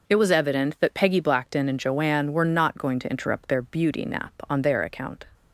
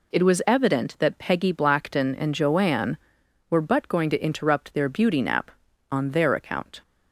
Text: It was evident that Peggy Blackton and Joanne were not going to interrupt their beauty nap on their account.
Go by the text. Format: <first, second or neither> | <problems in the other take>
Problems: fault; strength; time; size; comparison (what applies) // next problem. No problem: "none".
first | says "but" for "not"; at 3.6 s